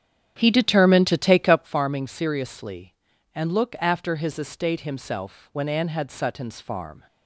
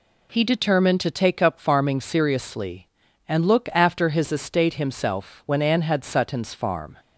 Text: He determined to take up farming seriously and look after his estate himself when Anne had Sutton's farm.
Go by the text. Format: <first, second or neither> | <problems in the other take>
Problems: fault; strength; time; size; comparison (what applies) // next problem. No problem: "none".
second | starts louder than the rest; strong; until 1.8 s; 9.5 dB